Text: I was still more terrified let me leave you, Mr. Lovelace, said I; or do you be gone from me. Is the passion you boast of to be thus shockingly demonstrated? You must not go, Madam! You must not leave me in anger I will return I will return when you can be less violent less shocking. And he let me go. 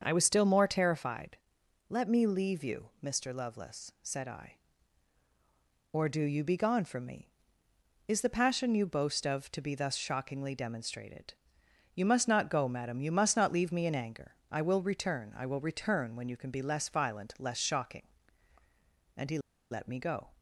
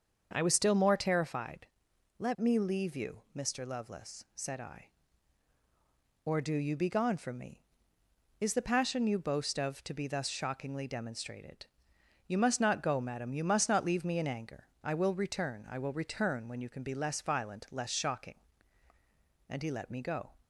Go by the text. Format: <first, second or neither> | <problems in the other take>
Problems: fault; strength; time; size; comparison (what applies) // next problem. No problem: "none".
second | starts louder than the rest; until 1.0 s; 6.5 dB; also in the second // pauses between "terrified" and "let"; noticeable; at 1.3 s; 0.52 s long; noticeable in the second // pauses between "anger" and "I"; slight; at 14.3 s; 0.16 s long; slight in the second // pauses between "he" and "let"; slight; at 19.3 s; 0.32 s long